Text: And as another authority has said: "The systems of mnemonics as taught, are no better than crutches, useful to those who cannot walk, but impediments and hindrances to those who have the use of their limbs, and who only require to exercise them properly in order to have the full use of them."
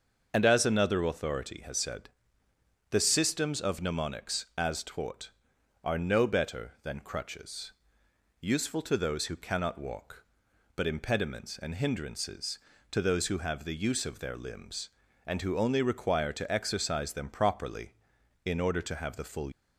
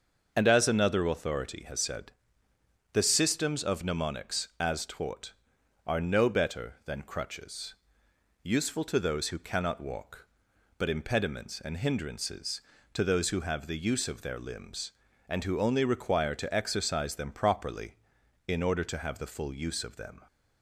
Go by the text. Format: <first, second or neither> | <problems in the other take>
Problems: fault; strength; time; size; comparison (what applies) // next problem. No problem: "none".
second | starts louder than the rest; until 1.3 s; 6.5 dB; also in the second // stops before "use of them"; at 19.5 s